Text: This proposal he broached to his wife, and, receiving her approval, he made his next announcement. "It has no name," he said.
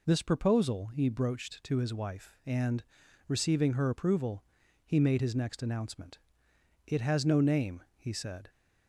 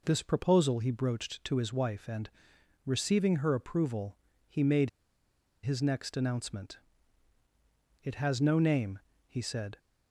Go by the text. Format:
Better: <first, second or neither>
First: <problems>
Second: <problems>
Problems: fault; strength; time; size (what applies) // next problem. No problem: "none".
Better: first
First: none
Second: pauses between "made" and "his"; noticeable; at 4.8 s; 0.74 s long